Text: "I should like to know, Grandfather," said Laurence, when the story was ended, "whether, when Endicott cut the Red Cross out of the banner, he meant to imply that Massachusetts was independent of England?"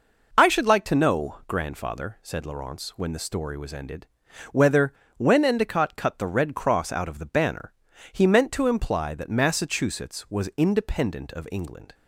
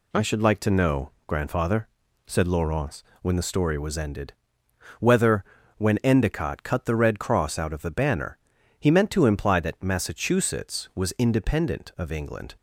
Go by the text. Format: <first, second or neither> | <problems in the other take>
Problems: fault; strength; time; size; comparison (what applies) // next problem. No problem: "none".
neither | none